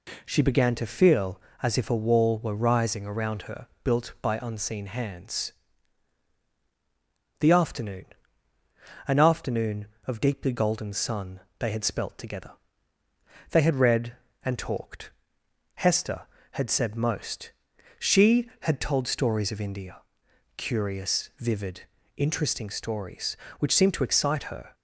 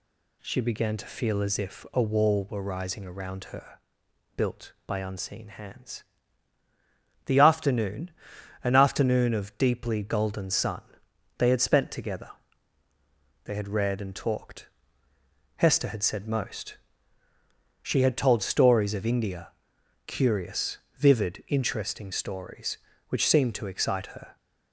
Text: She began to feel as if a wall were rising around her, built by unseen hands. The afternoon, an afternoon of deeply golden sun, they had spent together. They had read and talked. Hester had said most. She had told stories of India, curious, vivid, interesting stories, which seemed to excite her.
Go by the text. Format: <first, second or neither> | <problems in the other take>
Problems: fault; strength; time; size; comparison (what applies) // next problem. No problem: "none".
second | says "spelt" for "spent"; at 11.8 s